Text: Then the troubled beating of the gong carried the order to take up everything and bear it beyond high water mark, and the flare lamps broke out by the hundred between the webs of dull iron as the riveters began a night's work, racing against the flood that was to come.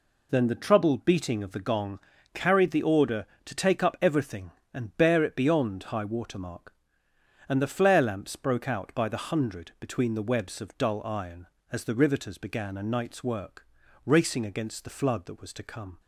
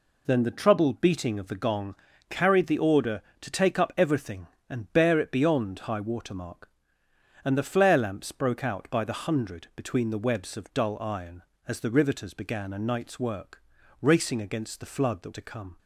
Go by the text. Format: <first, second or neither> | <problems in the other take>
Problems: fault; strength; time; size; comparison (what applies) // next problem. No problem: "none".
first | pauses between "gong" and "carried"; slight; at 1.9 s; 0.36 s long; slight in the first // skips "was"; at 15.3 s